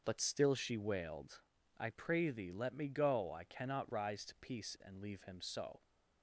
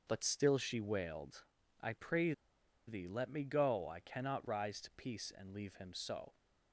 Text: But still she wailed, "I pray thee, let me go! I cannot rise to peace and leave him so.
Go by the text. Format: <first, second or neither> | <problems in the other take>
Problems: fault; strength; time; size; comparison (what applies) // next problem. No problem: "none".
first | starts louder than the rest; until 1.0 s; 6.5 dB; also in the first // pauses between "pray" and "thee"; noticeable; at 2.3 s; 0.55 s long